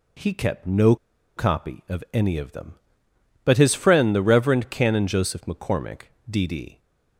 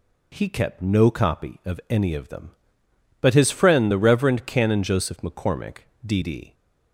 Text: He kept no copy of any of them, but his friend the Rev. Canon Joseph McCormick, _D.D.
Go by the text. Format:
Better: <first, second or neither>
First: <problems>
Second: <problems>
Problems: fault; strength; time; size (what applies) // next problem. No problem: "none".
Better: second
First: pauses between "no" and "copy"; at 0.9 s; 0.41 s long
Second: none